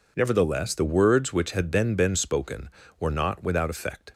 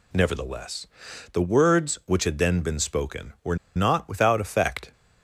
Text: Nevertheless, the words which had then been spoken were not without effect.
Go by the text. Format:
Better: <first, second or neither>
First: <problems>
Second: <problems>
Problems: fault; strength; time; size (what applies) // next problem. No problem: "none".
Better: first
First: none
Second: pauses between "were" and "not"; slight; at 3.5 s; 0.19 s long